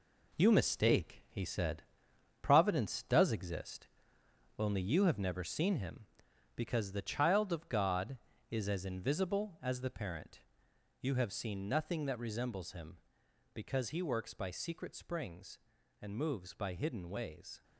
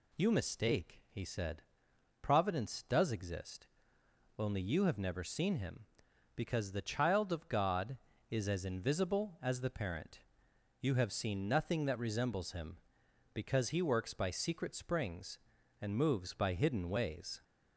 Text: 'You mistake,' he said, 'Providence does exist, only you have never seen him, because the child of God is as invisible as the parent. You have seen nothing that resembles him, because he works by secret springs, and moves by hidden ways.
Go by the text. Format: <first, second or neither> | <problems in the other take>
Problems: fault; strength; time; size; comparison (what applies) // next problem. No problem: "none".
second | gets quieter; throughout; 7 dB